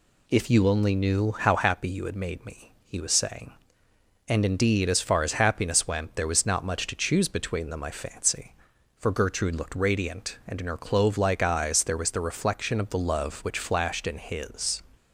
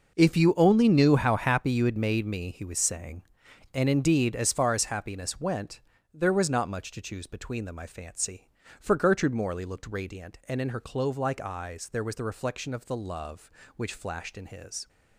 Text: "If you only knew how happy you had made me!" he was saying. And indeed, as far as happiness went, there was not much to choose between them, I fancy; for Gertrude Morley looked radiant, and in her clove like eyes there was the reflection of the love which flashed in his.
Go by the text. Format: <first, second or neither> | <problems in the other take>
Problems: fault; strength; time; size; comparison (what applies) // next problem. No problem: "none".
second | skips "Morley"; at 9.5 s